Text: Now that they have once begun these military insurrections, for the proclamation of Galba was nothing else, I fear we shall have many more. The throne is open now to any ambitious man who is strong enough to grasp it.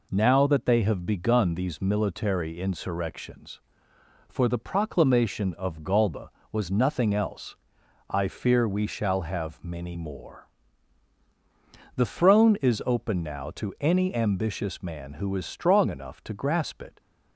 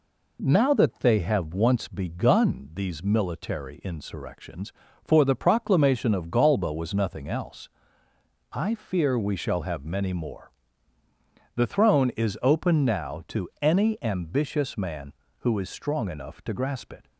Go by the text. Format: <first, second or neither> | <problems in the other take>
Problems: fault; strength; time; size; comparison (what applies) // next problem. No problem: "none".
second | skips "once"; at 1.0 s